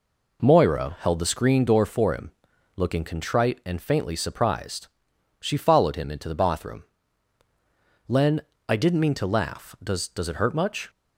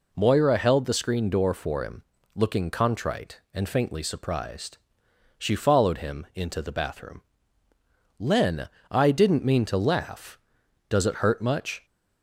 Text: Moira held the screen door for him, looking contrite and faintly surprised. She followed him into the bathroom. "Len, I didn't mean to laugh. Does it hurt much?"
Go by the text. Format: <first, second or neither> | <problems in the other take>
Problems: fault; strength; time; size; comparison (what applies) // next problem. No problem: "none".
second | says "Does" twice; at 10.0 s